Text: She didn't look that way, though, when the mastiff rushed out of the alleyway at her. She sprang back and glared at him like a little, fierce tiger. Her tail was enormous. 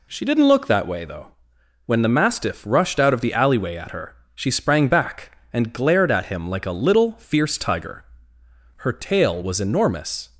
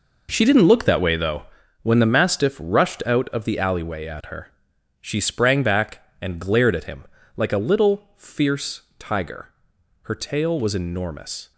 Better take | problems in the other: first | gets quieter; strong; throughout; 12 dB // pauses between "him" and "like"; slight; at 7.0 s; 0.32 s long // pauses between "fierce" and "tiger"; slight; at 8.8 s; 0.16 s long

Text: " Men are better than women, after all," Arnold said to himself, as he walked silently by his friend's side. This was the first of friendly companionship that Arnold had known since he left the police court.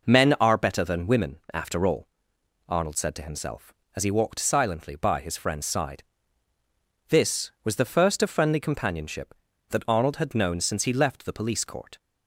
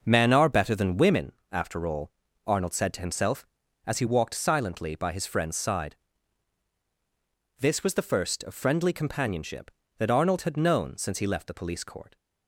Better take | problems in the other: neither | none

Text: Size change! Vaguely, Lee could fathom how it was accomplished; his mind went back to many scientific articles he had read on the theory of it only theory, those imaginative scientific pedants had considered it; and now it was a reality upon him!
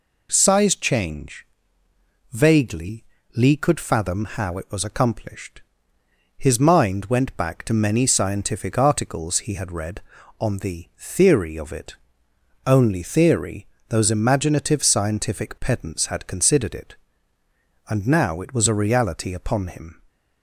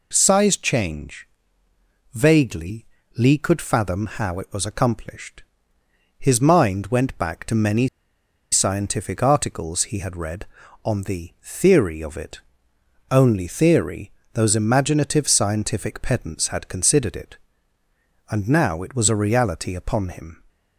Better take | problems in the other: first | pauses between "many" and "scientific"; noticeable; at 7.8 s; 0.64 s long // pauses between "it" and "only"; noticeable; at 12.4 s; 0.68 s long; noticeable in the first

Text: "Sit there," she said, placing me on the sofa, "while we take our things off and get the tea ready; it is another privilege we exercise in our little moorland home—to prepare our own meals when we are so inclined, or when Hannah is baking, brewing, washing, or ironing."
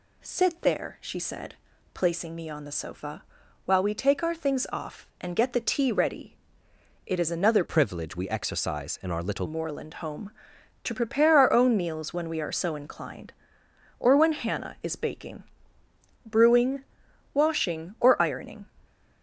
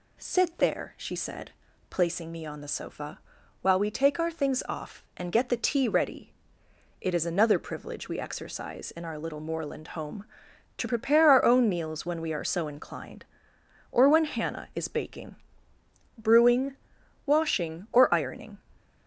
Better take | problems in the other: second | changes voice from "privilege" to "little"; from 7.6 to 9.4 s; 1.8 s long

